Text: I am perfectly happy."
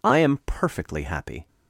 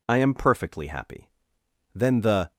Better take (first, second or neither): first